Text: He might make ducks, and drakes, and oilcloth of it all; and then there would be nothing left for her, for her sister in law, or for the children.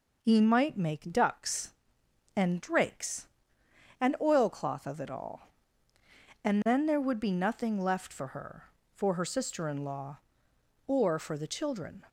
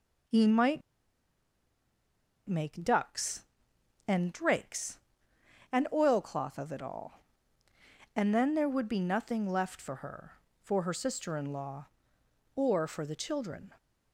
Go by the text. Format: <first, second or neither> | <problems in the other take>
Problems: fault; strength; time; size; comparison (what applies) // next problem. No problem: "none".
first | pauses between "might" and "make"; strong; at 0.8 s; 1.6 s long